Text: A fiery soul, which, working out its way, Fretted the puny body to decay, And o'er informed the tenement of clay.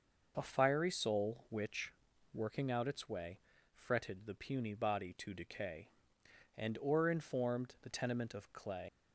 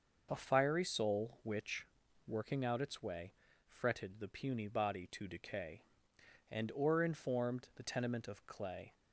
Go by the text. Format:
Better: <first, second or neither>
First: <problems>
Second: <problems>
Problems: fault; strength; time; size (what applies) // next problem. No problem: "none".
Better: second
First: leaves "clay" unfinished; at 8.8 s; 110 ms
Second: none